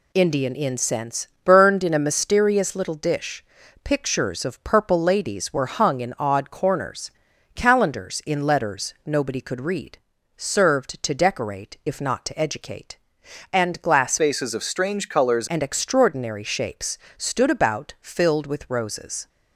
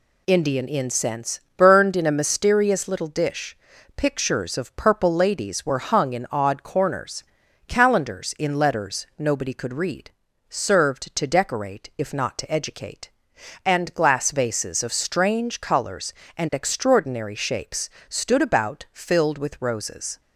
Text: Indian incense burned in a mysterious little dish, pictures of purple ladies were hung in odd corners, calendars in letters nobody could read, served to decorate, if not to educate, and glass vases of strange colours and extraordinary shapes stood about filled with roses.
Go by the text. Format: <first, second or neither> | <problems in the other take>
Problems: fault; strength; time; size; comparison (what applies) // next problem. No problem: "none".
second | pauses between "incense" and "burned"; slight; at 1.2 s; 0.18 s long; slight in the second // changes voice from "vases" to "colours"; from 14.1 to 15.4 s; 1.3 s long // pauses between "shapes" and "stood"; slight; at 16.9 s; 0.18 s long; slight in the second